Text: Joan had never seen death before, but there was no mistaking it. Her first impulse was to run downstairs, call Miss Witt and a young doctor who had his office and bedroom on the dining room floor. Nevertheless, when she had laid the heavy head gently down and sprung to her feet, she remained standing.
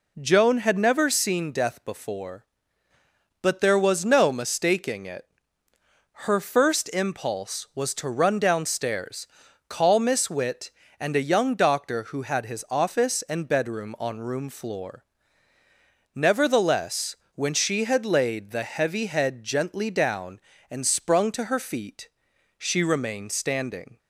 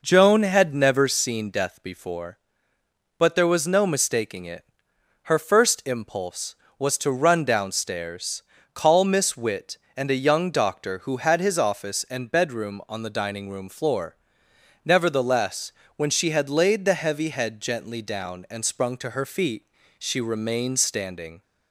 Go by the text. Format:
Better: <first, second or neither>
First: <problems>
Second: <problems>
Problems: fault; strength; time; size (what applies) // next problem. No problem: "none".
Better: second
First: skips "the dining"; at 14.1 s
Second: none